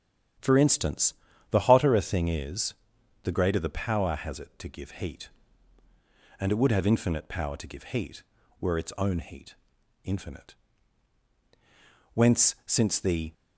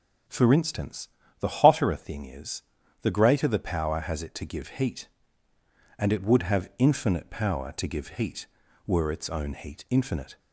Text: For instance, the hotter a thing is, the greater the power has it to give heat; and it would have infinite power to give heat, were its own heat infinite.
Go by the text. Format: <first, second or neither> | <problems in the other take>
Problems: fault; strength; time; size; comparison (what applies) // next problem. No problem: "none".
second | starts louder than the rest; strong; until 1.7 s; 9.5 dB // pauses between "heat" and "infinite"; noticeable; at 9.5 s; 0.50 s long // goes on to say "Whence since the"; noticeable; from 12.1 s on; 1.2 s long